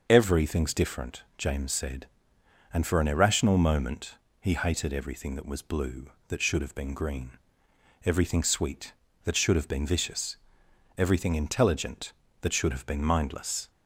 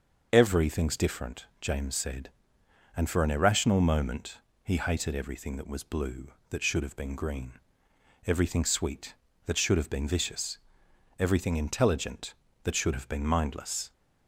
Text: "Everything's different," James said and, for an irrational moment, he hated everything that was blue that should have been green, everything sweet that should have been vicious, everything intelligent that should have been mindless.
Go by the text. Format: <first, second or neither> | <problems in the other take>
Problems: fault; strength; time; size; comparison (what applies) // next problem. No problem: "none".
neither | starts louder than the rest; the same in both